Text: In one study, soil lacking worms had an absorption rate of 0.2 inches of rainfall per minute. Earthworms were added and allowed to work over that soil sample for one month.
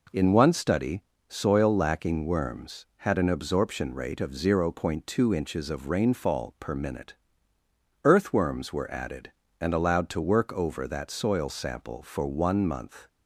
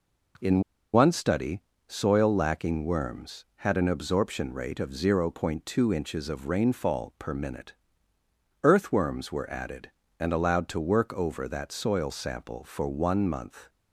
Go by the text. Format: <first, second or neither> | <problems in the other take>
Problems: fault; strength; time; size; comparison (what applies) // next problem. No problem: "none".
first | pauses between "In" and "one"; slight; at 0.6 s; 0.33 s long